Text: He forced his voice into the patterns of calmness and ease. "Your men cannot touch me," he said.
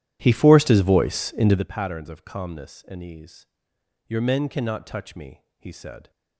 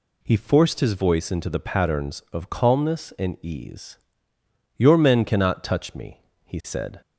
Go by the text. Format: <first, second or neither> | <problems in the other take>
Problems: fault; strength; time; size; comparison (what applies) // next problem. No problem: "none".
second | starts louder than the rest; strong; until 1.7 s; 12 dB